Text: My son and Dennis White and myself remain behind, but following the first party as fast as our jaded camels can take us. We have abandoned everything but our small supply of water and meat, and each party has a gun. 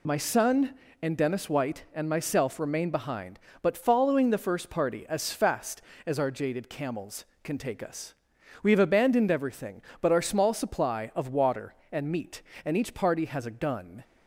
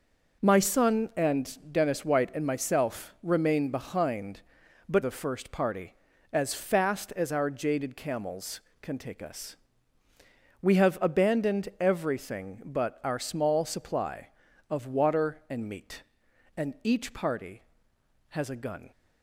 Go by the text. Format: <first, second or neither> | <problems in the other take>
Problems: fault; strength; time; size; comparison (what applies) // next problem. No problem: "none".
first | skips "following"; at 5.0 s